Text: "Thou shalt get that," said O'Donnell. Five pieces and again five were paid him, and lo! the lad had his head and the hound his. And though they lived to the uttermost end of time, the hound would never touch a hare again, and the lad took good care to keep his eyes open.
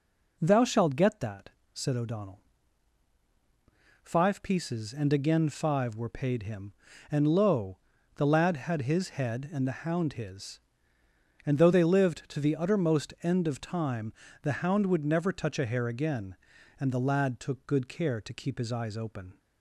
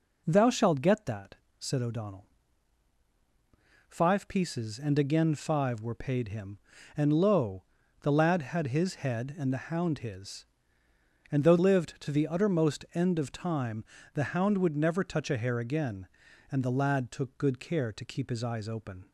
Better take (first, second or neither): first